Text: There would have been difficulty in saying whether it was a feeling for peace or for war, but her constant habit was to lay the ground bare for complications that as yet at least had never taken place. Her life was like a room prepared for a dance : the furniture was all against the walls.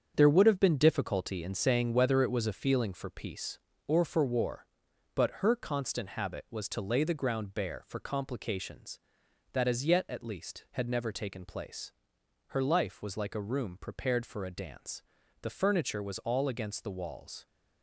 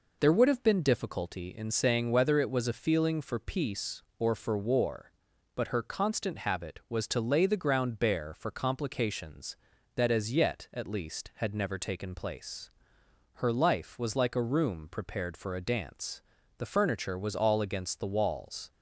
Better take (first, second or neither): second